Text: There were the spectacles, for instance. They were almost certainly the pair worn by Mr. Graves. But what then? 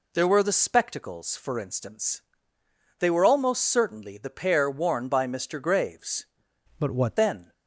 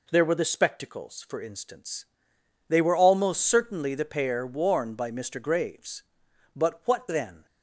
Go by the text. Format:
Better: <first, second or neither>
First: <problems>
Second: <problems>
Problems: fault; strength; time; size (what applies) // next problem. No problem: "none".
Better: second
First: changes voice from "But" to "what"; from 6.7 to 7.1 s; 0.4 s long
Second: none